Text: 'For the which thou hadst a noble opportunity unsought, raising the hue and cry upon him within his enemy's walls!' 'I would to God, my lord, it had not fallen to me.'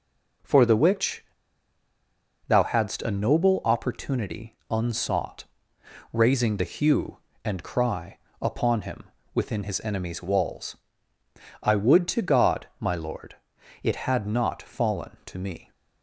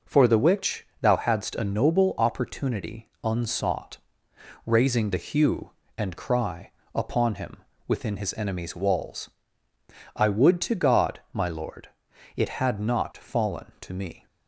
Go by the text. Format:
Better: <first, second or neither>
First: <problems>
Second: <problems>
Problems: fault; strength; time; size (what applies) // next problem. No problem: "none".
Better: second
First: pauses between "which" and "thou"; at 1.2 s; 1.2 s long // pauses between "cry" and "upon"; slight; at 8.1 s; 0.24 s long // pauses between "him" and "within"; slight; at 9.0 s; 0.30 s long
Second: pauses between "cry" and "upon"; slight; at 6.6 s; 0.24 s long // pauses between "him" and "within"; slight; at 7.5 s; 0.30 s long